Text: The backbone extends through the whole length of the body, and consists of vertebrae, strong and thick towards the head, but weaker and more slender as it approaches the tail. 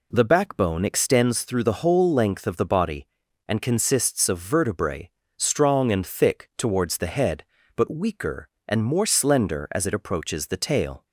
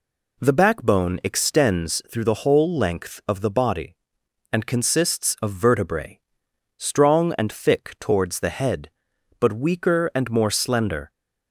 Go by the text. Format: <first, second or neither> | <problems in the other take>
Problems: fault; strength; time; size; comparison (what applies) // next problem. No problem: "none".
first | stops before "as it approaches the tail"; at 11.0 s